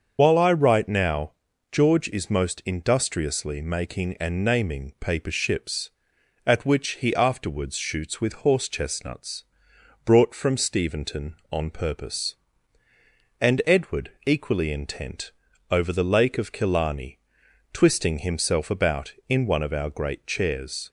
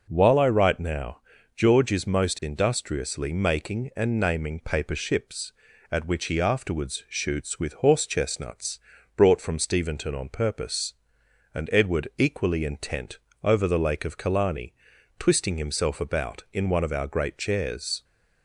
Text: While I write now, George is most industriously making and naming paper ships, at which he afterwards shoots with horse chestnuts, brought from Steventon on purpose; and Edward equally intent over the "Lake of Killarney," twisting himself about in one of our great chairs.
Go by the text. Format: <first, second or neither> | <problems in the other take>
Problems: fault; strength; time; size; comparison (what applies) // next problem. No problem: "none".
second | loses the start of "While"; at 0.1 s; 60 ms // starts louder than the rest; until 1.1 s; 7 dB // pauses between "Edward" and "equally"; slight; at 14.0 s; 0.16 s long // pauses between "intent" and "over"; at 15.3 s; 0.38 s long; slight in the second